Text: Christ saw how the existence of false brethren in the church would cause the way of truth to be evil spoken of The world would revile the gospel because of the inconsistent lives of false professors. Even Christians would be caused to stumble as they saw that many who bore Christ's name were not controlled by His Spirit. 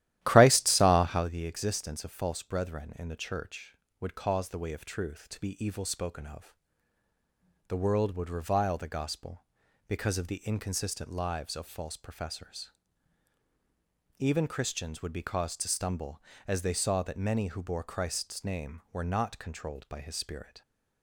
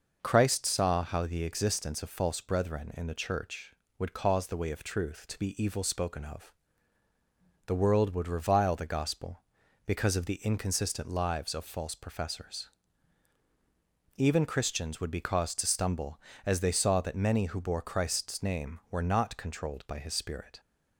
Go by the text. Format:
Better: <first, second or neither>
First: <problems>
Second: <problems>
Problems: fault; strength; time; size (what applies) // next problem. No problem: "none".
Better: second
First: starts louder than the rest; strong; until 1.4 s; 13.5 dB // pauses between "of" and "The"; at 6.5 s; 1.1 s long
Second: pauses between "of" and "The"; at 6.5 s; 1.1 s long